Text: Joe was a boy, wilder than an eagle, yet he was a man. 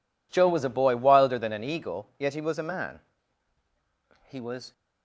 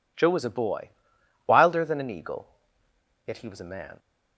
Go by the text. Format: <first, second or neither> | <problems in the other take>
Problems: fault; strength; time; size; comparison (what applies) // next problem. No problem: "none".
second | goes on to say "He was"; slight; from 4.2 s on; 0.44 s long